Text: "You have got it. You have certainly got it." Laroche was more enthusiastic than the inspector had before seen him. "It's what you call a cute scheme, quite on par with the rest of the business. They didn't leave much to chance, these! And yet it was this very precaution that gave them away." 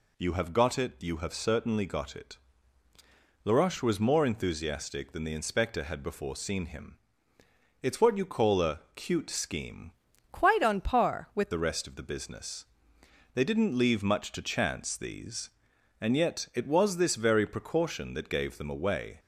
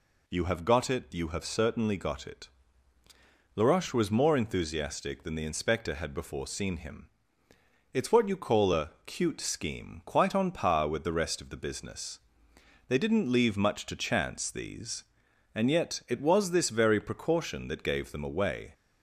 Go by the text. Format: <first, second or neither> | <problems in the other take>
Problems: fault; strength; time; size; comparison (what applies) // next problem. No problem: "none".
second | changes voice from "quite" to "with"; from 10.3 to 11.5 s; 1.2 s long